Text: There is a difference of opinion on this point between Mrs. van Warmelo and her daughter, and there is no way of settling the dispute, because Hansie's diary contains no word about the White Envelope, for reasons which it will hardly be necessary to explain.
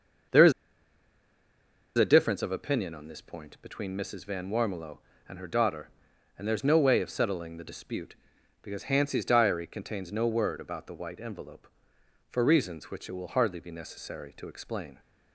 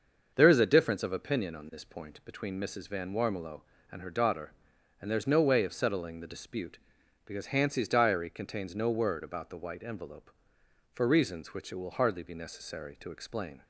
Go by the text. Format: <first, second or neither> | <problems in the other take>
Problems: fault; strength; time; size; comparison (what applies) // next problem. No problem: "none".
second | starts louder than the rest; until 2.7 s; 6.5 dB; also in the second // pauses between "is" and "a"; strong; at 0.5 s; 1.4 s long